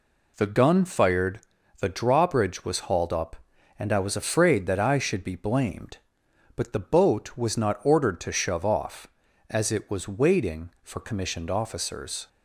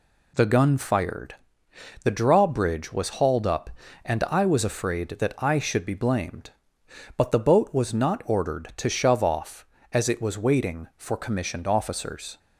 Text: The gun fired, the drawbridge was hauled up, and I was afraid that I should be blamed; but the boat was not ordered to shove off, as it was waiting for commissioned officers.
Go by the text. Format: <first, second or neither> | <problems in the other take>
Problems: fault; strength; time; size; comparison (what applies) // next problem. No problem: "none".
neither | none